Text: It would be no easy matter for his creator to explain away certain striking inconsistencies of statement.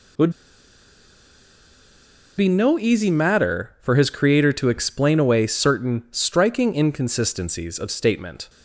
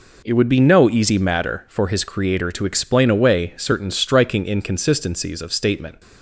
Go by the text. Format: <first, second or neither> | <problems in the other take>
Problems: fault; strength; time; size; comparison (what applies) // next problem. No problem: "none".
second | pauses between "would" and "be"; strong; at 0.3 s; 2.0 s long